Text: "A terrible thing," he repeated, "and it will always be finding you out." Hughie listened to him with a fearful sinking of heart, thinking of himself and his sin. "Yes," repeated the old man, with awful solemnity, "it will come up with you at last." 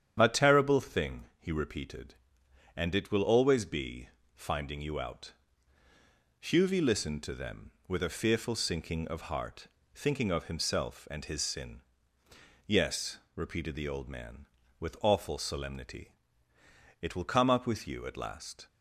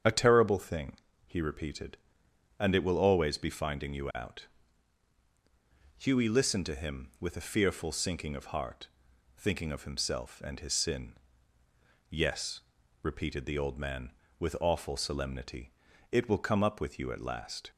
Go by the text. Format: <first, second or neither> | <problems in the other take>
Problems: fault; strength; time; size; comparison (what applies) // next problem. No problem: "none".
second | starts louder than the rest; strong; until 1.2 s; 9 dB; strong in the second // pauses between "be" and "finding"; slight; at 4.0 s; 0.26 s long // says "them" for "him"; at 7.3 s